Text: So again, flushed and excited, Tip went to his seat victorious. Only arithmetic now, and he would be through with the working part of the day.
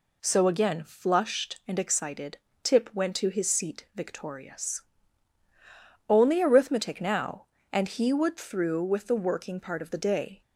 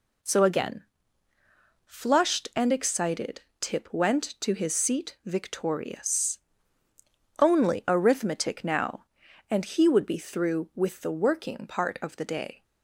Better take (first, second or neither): second